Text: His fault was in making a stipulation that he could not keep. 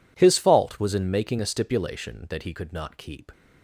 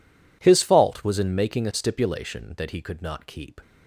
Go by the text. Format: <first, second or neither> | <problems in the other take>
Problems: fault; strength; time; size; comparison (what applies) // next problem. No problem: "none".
neither | none